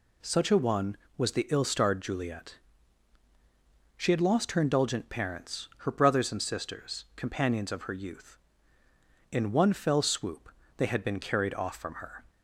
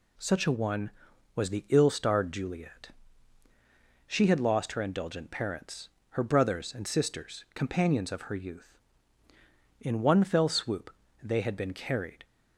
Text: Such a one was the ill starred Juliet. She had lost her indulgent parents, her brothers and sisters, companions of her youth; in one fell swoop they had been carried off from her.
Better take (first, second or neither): first